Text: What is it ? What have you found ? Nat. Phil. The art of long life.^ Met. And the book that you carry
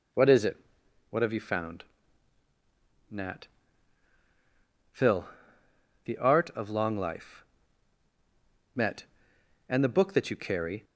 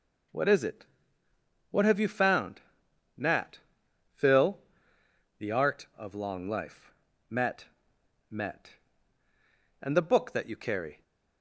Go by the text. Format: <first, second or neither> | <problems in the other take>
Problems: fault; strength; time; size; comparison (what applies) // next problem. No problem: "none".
first | says "Met" twice; at 8.3 s